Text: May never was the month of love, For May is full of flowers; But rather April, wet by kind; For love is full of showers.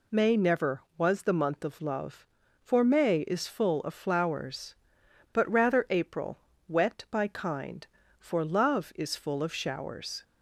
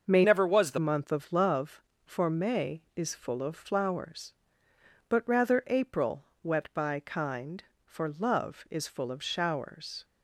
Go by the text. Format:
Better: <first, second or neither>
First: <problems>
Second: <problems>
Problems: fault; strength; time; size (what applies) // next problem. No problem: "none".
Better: first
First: none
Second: starts louder than the rest; until 1.0 s; 6.5 dB // changes voice from "never" to "the"; from 0.2 to 0.7 s; 0.5 s long